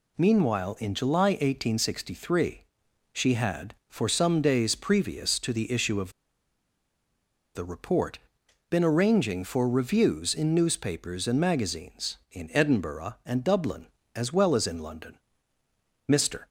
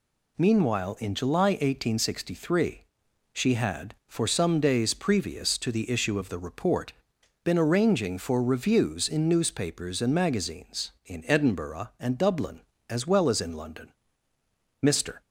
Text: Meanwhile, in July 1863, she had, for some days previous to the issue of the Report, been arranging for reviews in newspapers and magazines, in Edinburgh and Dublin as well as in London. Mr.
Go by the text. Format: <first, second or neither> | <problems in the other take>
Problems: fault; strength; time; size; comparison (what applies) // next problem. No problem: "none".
second | pauses between "of" and "the"; strong; at 6.1 s; 1.4 s long